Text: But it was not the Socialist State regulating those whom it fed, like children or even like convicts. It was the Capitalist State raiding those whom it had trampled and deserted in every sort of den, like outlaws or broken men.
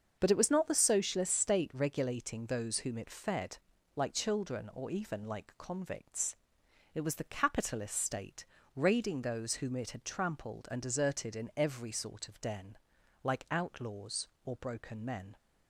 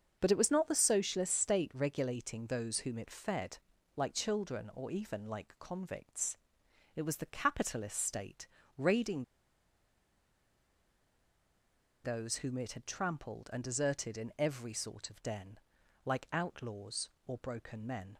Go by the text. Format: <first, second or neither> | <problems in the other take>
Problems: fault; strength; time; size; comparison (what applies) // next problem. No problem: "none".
first | starts louder than the rest; until 1.2 s; 6.5 dB; also in the first // pauses between "State" and "raiding"; slight; at 8.4 s; 0.32 s long; slight in the first // pauses between "raiding" and "those"; strong; at 9.2 s; 2.8 s long